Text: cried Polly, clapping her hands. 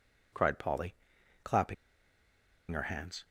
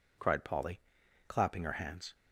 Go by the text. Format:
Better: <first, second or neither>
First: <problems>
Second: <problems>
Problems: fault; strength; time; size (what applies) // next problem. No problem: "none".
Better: second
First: pauses between "clapping" and "her"; noticeable; at 1.7 s; 0.96 s long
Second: none